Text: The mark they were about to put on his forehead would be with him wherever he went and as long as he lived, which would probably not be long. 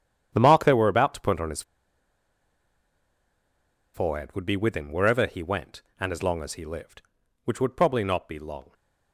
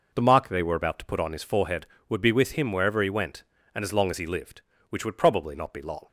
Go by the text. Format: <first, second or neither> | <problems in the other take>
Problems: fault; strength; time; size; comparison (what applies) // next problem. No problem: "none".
second | starts louder than the rest; strong; until 1.3 s; 9.5 dB // pauses between "his" and "forehead"; strong; at 1.6 s; 2.3 s long